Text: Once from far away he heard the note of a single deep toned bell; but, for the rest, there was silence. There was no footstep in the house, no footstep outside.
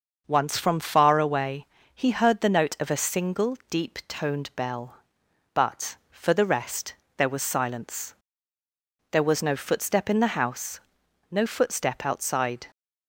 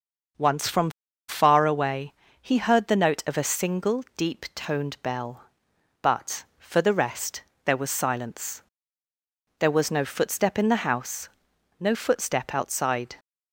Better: first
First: starts louder than the rest; noticeable; until 1.2 s; 6 dB // pauses between "away" and "he"; slight; at 1.6 s; 0.28 s long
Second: starts louder than the rest; noticeable; until 1.7 s; 6 dB // pauses between "from" and "far"; at 0.9 s; 0.37 s long // pauses between "away" and "he"; slight; at 2.1 s; 0.28 s long

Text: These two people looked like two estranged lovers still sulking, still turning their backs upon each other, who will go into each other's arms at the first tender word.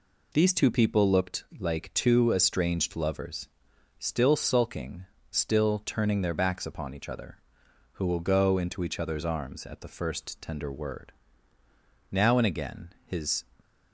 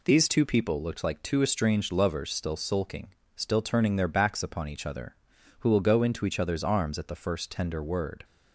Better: second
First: pauses between "looked" and "like"; slight; at 1.4 s; 0.16 s long // pauses between "lovers" and "still"; noticeable; at 3.4 s; 0.52 s long // goes on to say "Now and again his"; from 12.1 s on; 1.3 s long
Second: none

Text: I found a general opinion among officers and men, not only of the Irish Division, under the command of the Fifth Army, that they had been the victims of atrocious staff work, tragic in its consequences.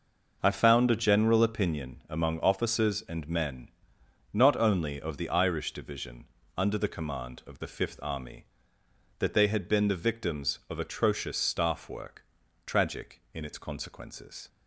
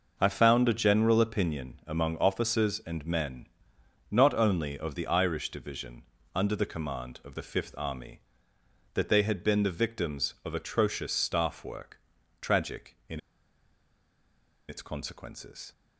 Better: first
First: none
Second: pauses between "in" and "its"; strong; at 13.1 s; 1.4 s long

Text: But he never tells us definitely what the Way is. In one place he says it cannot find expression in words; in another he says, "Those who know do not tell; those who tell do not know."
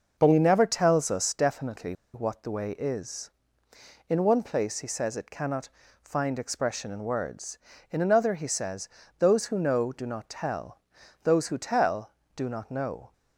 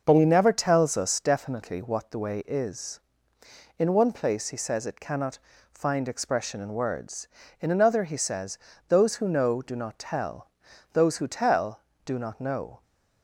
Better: second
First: pauses between "definitely" and "what"; slight; at 1.9 s; 0.19 s long // pauses between "cannot" and "find"; slight; at 5.6 s; 0.34 s long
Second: pauses between "cannot" and "find"; slight; at 5.3 s; 0.34 s long

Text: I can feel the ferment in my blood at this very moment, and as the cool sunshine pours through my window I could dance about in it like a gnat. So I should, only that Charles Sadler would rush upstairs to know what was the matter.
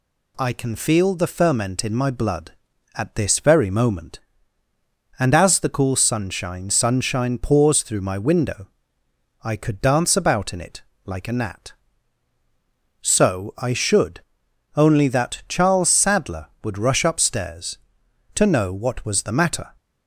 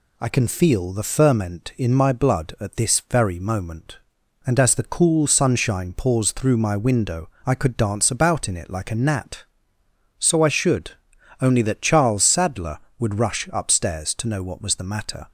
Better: second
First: says "sunshine" twice; at 6.6 s // pauses between "window" and "I"; noticeable; at 8.6 s; 0.74 s long // pauses between "it" and "like"; slight; at 10.8 s; 0.24 s long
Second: pauses between "window" and "I"; slight; at 7.2 s; 0.16 s long

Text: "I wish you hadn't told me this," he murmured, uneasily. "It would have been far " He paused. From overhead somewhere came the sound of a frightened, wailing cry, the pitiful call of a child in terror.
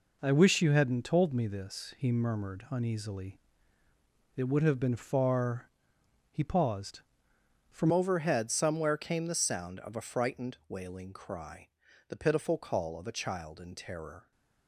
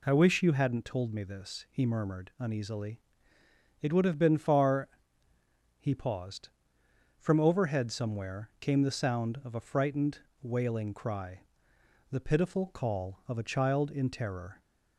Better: second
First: changes voice at "overhead"; from 7.9 s on; 6.4 s long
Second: none

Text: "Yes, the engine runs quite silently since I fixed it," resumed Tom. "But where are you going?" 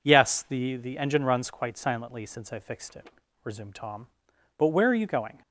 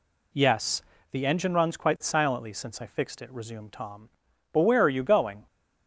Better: second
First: says "the" twice; at 0.7 s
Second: none

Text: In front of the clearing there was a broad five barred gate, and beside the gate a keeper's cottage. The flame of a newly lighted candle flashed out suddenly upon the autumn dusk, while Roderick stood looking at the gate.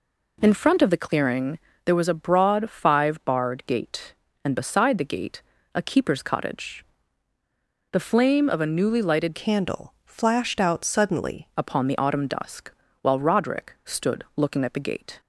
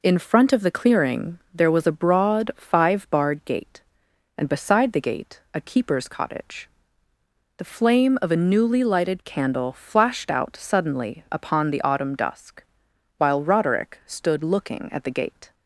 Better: second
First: pauses between "clearing" and "there"; slight; at 1.5 s; 0.24 s long // pauses between "gate" and "a"; slight; at 5.4 s; 0.34 s long // changes voice from "candle" to "suddenly"; from 9.3 to 11.4 s; 2.1 s long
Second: pauses between "clearing" and "there"; slight; at 1.3 s; 0.16 s long

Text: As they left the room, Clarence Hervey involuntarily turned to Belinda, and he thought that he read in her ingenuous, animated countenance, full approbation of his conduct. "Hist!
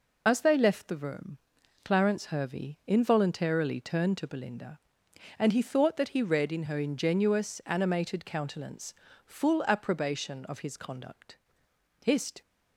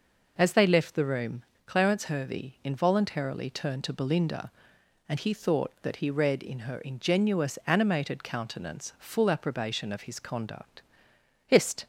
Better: second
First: loses the start of "As"; at 0.2 s; 35 ms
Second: none

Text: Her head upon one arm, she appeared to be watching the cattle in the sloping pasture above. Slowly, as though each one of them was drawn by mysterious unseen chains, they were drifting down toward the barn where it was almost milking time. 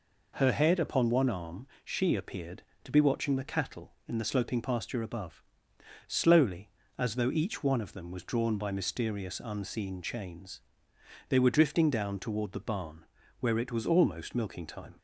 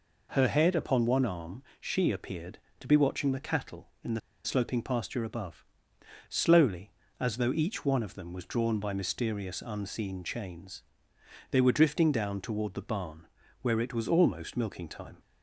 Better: first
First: pauses between "barn" and "where"; slight; at 13.0 s; 0.36 s long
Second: pauses between "the" and "sloping"; slight; at 4.1 s; 0.24 s long // pauses between "barn" and "where"; slight; at 13.2 s; 0.36 s long

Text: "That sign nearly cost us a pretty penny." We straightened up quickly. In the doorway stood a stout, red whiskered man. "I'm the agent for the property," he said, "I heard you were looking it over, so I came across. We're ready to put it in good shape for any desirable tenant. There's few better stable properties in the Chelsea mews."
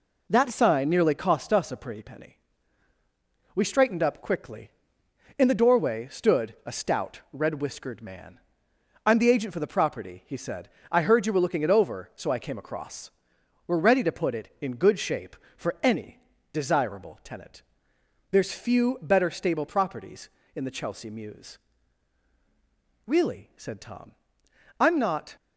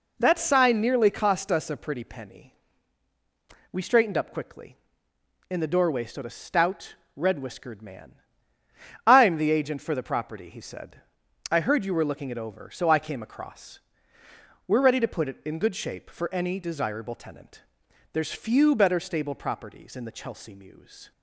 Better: second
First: pauses between "any" and "desirable"; slight; at 16.1 s; 0.32 s long // goes on to say "Really said Tom I'm not"; strong; from 23.0 s on; 2.3 s long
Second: none

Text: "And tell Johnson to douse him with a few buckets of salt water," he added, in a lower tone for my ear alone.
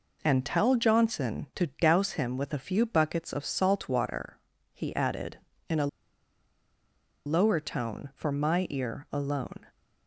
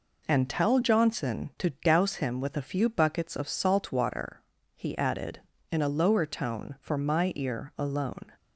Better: second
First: pauses between "a" and "lower"; strong; at 5.8 s; 1.3 s long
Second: none

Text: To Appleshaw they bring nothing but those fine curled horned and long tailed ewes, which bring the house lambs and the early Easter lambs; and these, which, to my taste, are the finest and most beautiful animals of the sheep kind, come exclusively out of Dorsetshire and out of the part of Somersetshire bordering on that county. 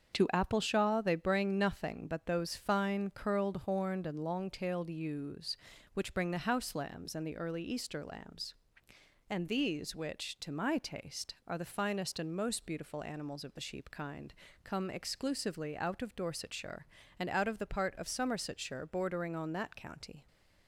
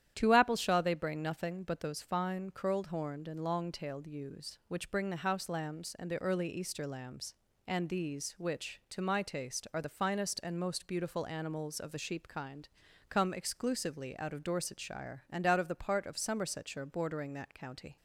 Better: first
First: starts louder than the rest; until 1.1 s; 7 dB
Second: starts louder than the rest; strong; until 1.1 s; 10.5 dB // skips "on"; at 17.3 s

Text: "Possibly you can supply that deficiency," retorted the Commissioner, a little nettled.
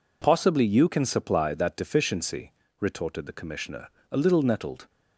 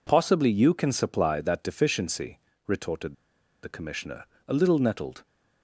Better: first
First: none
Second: pauses between "retorted" and "the"; noticeable; at 3.1 s; 0.49 s long

